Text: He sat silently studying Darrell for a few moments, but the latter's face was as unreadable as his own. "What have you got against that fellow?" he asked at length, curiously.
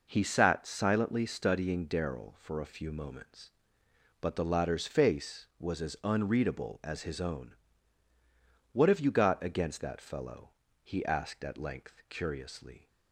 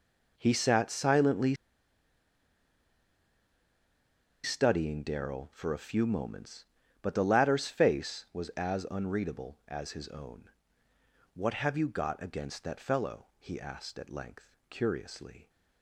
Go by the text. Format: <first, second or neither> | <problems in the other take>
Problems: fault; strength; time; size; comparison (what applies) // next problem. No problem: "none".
first | pauses between "silently" and "studying"; strong; at 1.5 s; 2.8 s long